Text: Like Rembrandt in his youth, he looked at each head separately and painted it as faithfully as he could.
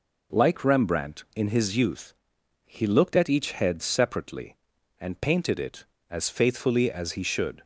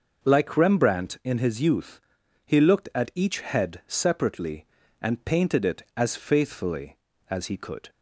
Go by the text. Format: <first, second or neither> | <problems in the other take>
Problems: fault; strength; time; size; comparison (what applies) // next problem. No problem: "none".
second | says "should" for "could"; at 7.2 s